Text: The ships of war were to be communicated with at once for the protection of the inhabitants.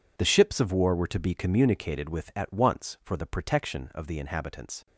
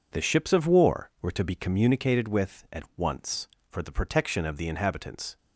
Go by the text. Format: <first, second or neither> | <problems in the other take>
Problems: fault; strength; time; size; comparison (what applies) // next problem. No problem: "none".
second | gets quieter; strong; throughout; 15.5 dB